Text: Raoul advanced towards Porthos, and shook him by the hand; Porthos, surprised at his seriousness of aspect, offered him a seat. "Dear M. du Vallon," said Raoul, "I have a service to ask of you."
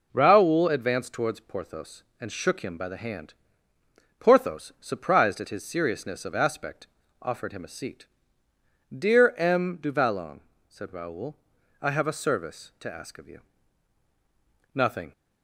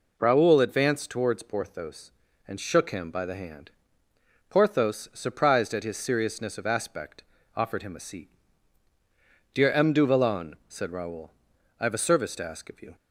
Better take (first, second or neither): second